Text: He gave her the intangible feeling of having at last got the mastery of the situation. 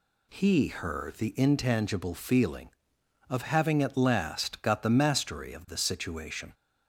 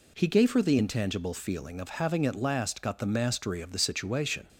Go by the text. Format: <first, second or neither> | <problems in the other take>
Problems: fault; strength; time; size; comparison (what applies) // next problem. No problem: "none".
second | skips "gave"; at 0.6 s